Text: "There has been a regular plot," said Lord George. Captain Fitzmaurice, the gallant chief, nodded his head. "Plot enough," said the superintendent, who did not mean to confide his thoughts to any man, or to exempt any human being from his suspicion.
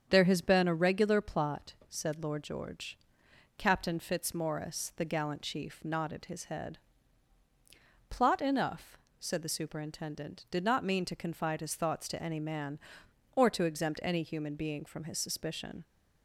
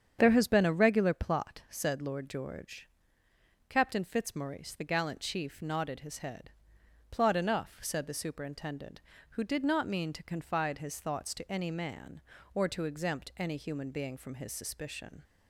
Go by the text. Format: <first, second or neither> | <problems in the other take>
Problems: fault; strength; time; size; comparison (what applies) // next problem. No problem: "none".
second | starts louder than the rest; strong; until 1.1 s; 7.5 dB; strong in the second // skips "who"; at 10.4 s